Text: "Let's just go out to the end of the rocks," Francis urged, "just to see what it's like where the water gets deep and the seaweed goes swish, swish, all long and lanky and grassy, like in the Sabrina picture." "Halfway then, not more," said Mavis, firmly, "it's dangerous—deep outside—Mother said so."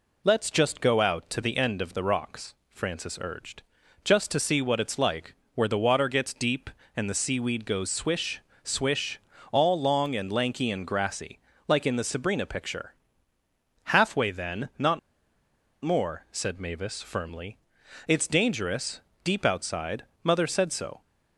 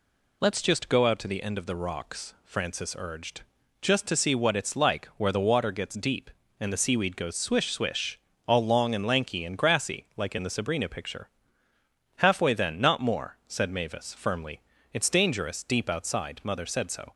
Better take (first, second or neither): second